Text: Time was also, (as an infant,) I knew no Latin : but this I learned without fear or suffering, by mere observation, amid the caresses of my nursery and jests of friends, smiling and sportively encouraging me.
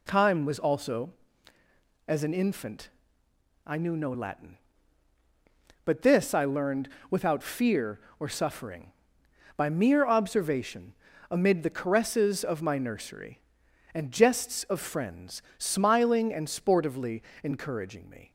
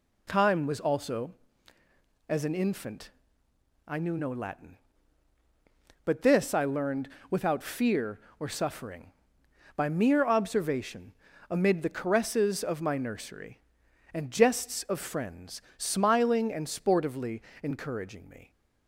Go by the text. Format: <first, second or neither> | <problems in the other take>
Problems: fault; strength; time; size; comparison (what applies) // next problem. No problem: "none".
neither | pauses between "learned" and "without"; slight; the same in both // pauses between "sportively" and "encouraging"; slight; the same in both